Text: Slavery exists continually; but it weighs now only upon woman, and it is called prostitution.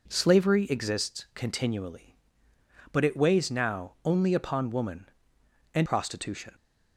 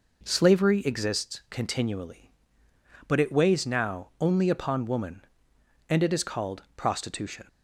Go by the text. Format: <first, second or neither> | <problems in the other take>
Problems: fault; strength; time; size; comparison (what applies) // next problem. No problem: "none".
second | skips "it is called"; at 5.8 s